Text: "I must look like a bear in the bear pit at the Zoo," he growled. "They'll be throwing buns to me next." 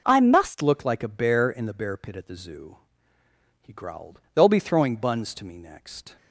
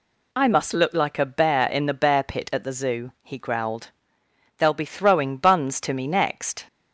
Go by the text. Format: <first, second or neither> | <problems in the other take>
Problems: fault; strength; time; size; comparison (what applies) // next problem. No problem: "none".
second | changes voice at "look"; from 0.6 s on; 5.5 s long